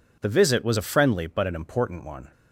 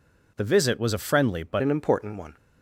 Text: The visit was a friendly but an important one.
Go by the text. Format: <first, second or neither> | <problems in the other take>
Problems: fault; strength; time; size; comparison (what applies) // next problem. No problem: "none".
first | changes voice at "an"; from 1.6 s on; 0.7 s long